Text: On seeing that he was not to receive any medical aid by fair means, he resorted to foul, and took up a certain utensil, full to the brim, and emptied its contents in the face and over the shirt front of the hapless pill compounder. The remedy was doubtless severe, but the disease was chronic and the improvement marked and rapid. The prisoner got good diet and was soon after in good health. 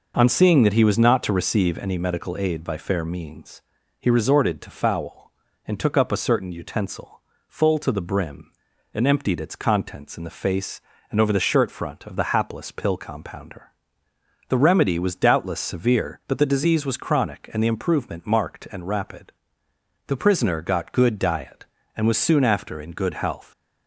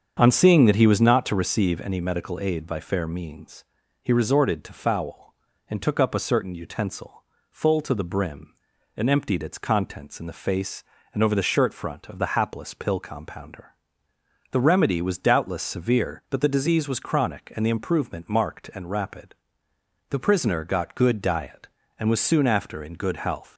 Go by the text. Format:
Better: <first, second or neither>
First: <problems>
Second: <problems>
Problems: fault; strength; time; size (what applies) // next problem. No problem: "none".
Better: first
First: none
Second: starts louder than the rest; strong; until 1.2 s; 7.5 dB